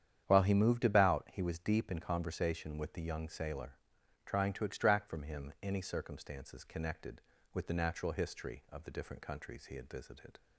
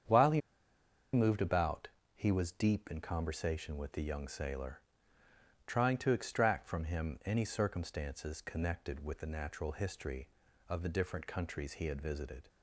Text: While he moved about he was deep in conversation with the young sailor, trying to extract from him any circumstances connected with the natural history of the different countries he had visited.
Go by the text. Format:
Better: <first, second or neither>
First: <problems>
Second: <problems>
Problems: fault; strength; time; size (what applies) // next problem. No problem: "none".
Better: first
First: starts louder than the rest; strong; until 1.2 s; 9 dB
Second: starts louder than the rest; strong; until 1.8 s; 8 dB // pauses between "he" and "moved"; noticeable; at 0.4 s; 0.72 s long // pauses between "about" and "he"; slight; at 1.8 s; 0.26 s long